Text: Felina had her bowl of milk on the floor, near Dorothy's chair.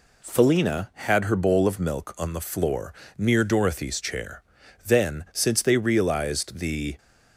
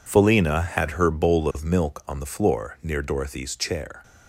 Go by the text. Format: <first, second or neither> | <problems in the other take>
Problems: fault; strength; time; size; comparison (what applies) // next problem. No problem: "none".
second | goes on to say "Then since they realized the"; strong; from 4.8 s on; 2.1 s long